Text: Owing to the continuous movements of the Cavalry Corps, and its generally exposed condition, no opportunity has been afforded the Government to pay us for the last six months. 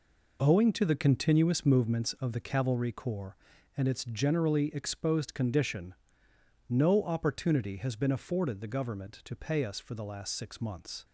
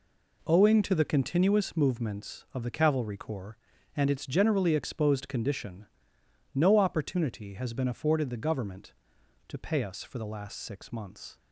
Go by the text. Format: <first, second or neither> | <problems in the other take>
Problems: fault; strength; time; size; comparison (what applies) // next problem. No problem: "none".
neither | none